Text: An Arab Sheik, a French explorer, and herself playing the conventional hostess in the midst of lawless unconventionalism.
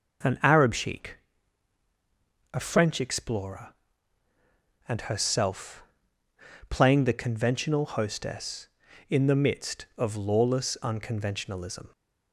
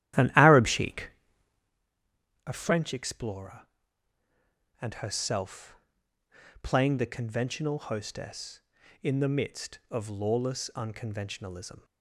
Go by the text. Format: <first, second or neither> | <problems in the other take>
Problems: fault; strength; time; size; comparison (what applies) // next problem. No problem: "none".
first | starts louder than the rest; strong; until 1.8 s; 12.5 dB // pauses between "herself" and "playing"; noticeable; at 5.7 s; 0.88 s long; noticeable in the first